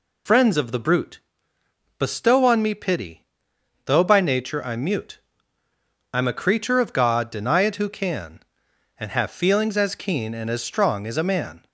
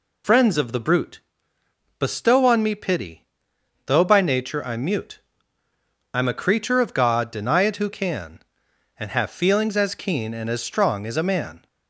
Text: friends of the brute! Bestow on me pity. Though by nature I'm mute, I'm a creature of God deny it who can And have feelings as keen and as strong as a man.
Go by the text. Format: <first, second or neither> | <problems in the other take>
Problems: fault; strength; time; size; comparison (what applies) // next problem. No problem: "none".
neither | none